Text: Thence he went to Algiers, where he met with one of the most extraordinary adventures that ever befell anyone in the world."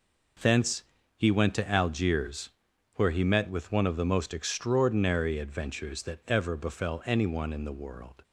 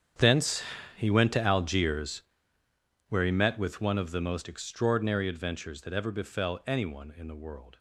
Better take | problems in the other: first | gets quieter; strong; throughout; 17 dB // pauses between "Thence" and "he"; slight; at 0.6 s; 0.32 s long; slight in the first

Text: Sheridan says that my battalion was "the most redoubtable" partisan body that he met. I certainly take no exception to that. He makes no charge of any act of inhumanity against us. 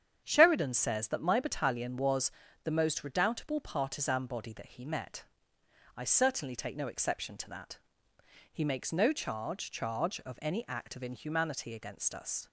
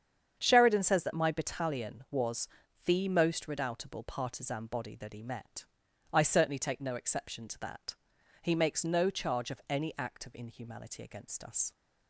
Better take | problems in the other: second | starts louder than the rest; strong; until 1.2 s; 8 dB; strong in the second // pauses between "was" and "the"; slight; at 2.3 s; 0.32 s long; also in the second // says "charge" twice; at 9.6 s

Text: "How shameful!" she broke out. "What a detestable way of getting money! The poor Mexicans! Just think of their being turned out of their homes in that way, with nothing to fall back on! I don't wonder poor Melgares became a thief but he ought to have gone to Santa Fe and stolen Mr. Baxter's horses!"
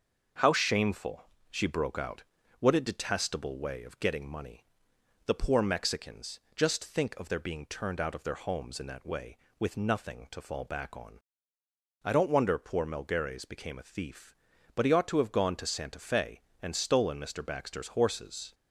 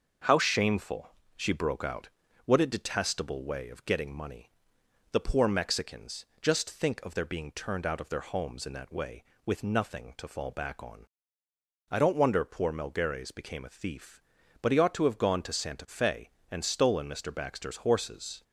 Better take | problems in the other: neither | starts louder than the rest; noticeable; the same in both

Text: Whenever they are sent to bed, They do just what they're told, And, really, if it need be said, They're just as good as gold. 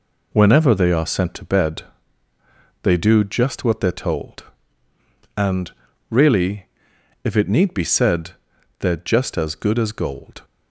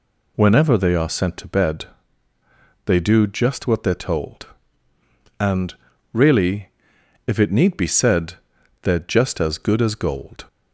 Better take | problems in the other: second | gets quieter; throughout; 6.5 dB

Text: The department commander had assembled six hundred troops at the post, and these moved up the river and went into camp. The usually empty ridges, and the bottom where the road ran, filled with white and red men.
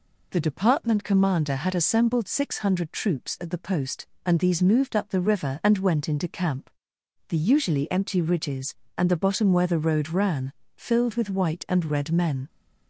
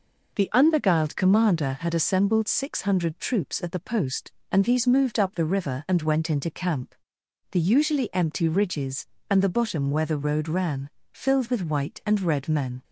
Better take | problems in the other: first | says "unbeguiled" for "department"; at 0.5 s

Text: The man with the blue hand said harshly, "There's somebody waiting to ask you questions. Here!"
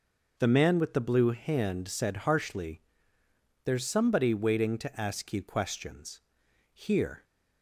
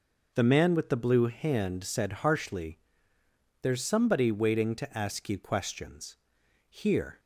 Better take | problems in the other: neither | none

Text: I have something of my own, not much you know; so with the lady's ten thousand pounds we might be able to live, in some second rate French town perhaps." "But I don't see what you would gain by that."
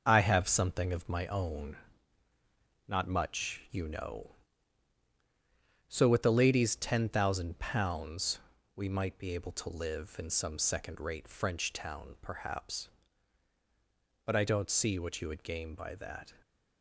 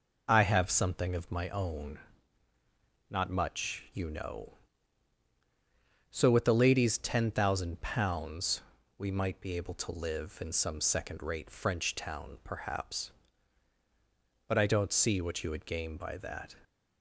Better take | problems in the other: second | gets quieter; noticeable; throughout; 6 dB // pauses between "pounds" and "we"; at 8.3 s; 0.38 s long; also in the second

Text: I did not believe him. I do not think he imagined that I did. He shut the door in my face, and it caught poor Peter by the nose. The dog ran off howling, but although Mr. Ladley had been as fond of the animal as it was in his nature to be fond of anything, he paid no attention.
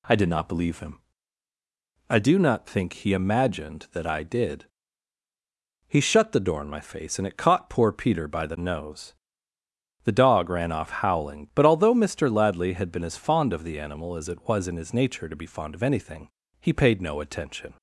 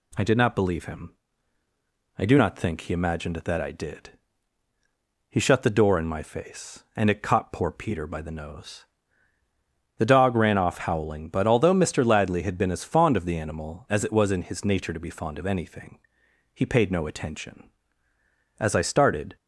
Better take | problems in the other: first | goes on to say "As I started"; noticeable; from 18.5 s on; 0.78 s long

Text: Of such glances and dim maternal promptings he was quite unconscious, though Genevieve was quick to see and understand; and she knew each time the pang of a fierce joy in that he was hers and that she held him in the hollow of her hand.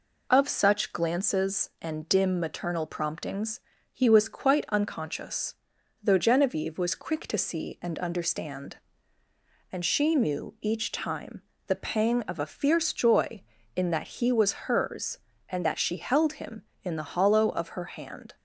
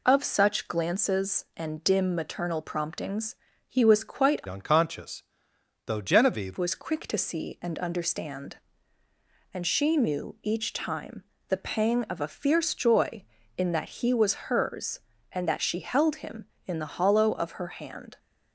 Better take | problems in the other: first | pauses between "promptings" and "he"; slight; at 3.3 s; 0.32 s long; slight in the first // changes voice from "unconscious" to "Genevieve"; from 4.4 to 6.5 s; 2.1 s long // pauses between "time" and "the"; slight; at 11.2 s; 0.26 s long; slight in the first

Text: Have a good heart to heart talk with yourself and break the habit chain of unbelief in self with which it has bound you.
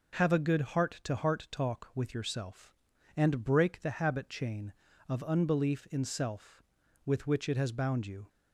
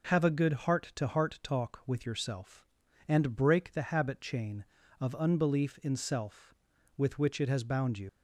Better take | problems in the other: first | leaves "you" unfinished; at 8.0 s; 100 ms

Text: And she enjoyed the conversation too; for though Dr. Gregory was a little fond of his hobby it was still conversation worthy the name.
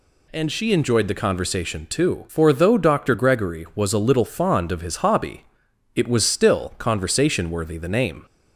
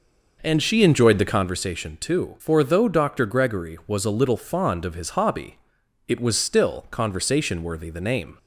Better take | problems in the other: first | starts louder than the rest; noticeable; until 1.5 s; 5.5 dB // pauses between "hobby" and "it"; noticeable; at 5.5 s; 0.48 s long; noticeable in the first

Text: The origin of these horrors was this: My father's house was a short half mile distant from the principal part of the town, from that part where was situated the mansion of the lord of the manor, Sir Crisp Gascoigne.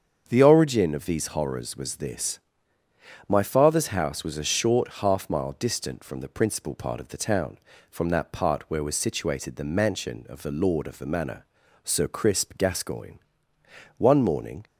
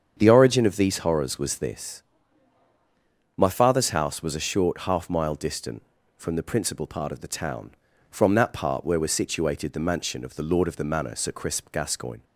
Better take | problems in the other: second | starts louder than the rest; strong; until 1.2 s; 7 dB; strong in the second // goes on to say "One morning"; noticeable; from 13.9 s on; 0.68 s long

